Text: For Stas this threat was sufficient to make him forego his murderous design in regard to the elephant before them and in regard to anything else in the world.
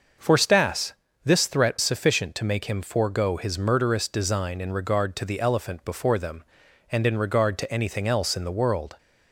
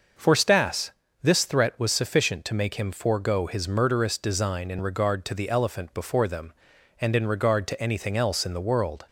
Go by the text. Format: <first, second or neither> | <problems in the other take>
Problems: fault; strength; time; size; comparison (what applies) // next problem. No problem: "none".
second | starts louder than the rest; noticeable; until 1.5 s; 6 dB; also in the second // pauses between "Stas" and "this"; slight; at 0.9 s; 0.30 s long; slight in the second // skips "was"; at 1.7 s